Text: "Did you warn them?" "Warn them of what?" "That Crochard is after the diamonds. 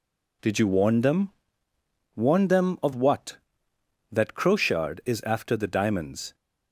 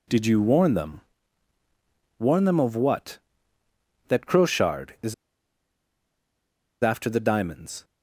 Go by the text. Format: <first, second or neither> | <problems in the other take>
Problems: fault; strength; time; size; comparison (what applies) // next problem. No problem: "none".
first | pauses between "is" and "after"; strong; at 5.1 s; 1.6 s long